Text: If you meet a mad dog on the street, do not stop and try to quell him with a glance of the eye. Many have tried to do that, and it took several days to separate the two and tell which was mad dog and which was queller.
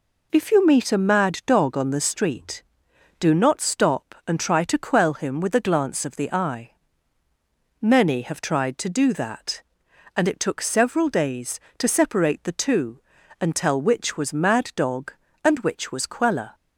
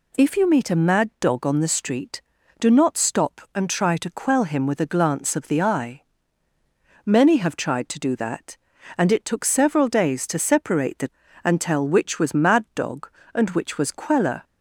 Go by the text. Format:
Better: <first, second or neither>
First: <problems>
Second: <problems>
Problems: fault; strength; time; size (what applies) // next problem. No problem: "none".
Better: first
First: none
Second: skips "two"; at 11.2 s